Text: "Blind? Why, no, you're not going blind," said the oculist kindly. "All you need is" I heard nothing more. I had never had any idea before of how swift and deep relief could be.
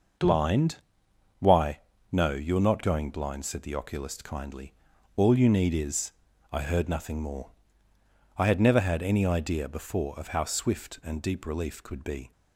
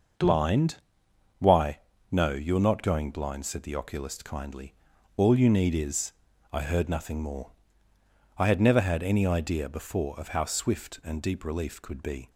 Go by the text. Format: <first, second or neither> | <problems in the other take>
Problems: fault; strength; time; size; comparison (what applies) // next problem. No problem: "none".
neither | starts louder than the rest; noticeable; the same in both // pauses between "is" and "I"; the same in both